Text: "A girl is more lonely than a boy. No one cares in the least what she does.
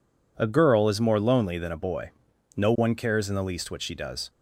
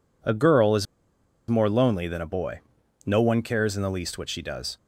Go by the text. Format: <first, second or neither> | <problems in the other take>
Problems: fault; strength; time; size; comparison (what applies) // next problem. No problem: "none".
first | pauses between "is" and "more"; noticeable; at 0.8 s; 0.63 s long